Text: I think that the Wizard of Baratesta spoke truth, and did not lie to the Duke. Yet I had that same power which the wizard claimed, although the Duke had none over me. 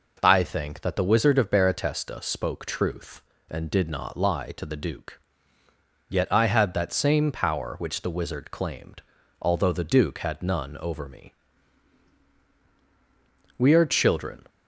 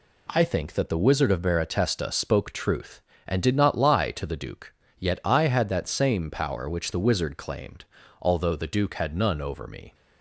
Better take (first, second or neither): second